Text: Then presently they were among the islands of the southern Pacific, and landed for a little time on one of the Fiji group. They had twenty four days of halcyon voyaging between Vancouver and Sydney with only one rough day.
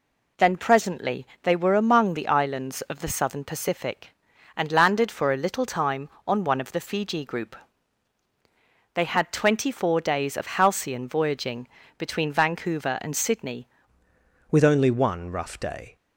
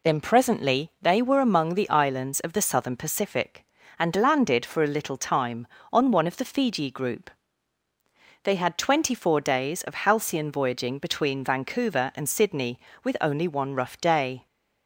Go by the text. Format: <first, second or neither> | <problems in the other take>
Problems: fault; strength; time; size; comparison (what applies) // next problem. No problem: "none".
second | pauses between "presently" and "they"; slight; at 1.2 s; 0.16 s long // pauses between "voyaging" and "between"; slight; at 11.6 s; 0.30 s long // changes voice at "with"; from 14.5 s on; 1.4 s long